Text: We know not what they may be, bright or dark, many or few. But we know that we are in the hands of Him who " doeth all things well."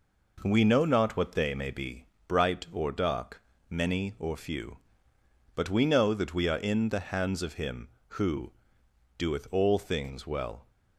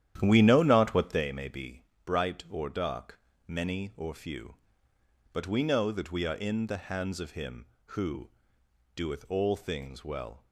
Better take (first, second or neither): first